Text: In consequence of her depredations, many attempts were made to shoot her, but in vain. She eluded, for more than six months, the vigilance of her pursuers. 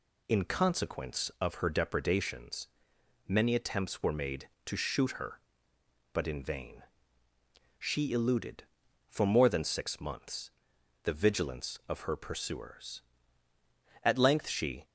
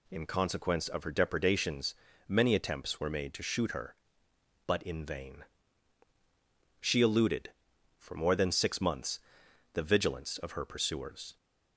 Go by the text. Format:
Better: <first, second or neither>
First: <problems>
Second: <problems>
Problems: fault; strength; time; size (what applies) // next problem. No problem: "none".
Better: second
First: goes on to say "At length she"; noticeable; from 14.0 s on; 0.82 s long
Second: none